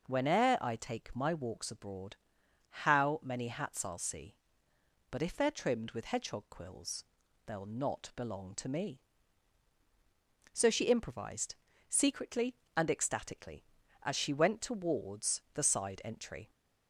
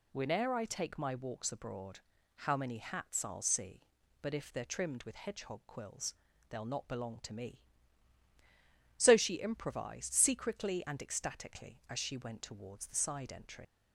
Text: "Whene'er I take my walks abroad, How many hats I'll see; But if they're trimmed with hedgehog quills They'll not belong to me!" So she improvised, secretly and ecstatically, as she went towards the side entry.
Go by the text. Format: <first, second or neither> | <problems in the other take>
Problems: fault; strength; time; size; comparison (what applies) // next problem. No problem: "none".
first | pauses between "quills" and "They'll"; slight; at 6.1 s; 0.34 s long; also in the first // leaves "entry" unfinished; at 13.6 s; 65 ms